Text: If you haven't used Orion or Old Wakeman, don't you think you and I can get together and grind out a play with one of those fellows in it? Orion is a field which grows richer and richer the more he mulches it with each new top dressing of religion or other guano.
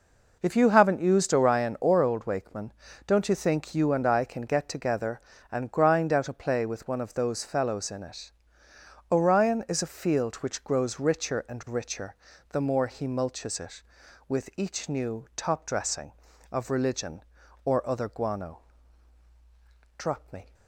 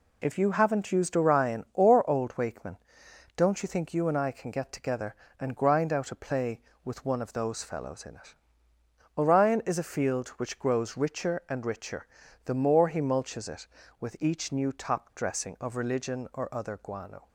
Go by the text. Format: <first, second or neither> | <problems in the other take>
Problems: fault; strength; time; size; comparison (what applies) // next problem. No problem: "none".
second | pauses between "richer" and "the"; slight; at 12.1 s; 0.34 s long; also in the second // goes on to say "Drop me"; from 19.9 s on; 0.58 s long